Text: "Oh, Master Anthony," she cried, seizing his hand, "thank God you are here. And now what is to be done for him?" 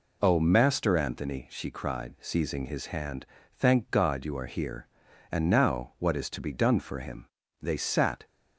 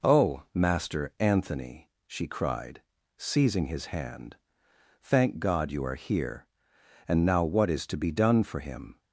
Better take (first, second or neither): second